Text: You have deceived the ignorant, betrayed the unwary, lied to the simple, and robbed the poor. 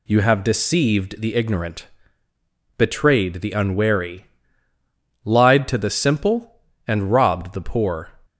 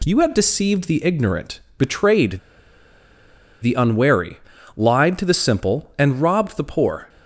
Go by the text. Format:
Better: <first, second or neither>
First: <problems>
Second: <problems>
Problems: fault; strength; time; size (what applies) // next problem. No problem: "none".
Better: first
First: none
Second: pauses between "betrayed" and "the"; at 2.3 s; 1.2 s long